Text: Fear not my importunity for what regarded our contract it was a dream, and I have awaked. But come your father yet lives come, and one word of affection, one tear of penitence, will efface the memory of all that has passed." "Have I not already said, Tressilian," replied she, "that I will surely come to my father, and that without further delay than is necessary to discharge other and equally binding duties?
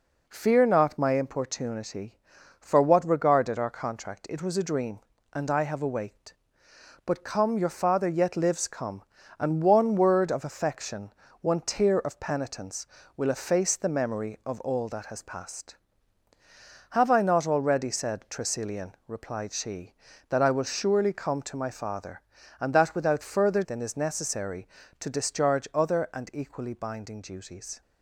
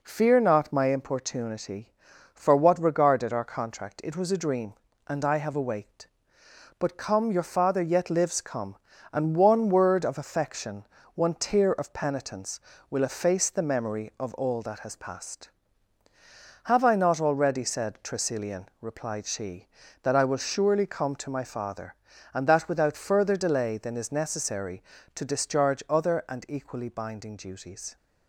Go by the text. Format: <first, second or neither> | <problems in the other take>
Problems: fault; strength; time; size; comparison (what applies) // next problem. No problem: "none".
second | skips "delay"; at 23.6 s